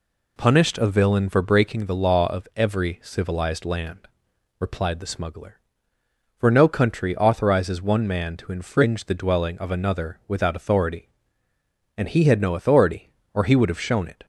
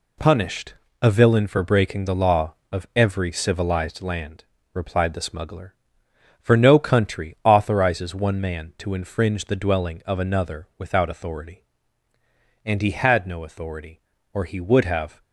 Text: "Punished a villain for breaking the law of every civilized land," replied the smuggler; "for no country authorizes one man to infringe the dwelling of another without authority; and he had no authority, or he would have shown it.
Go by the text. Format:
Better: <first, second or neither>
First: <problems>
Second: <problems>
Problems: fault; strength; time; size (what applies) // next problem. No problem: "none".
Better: first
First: none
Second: pauses between "Punished" and "a"; slight; at 0.7 s; 0.28 s long // stops before "shown it"; at 15.2 s